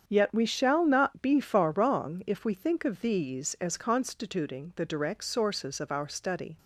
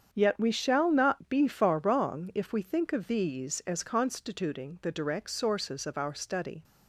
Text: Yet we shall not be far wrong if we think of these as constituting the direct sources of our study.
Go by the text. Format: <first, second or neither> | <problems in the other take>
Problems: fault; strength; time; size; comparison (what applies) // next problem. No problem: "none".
neither | starts louder than the rest; strong; the same in both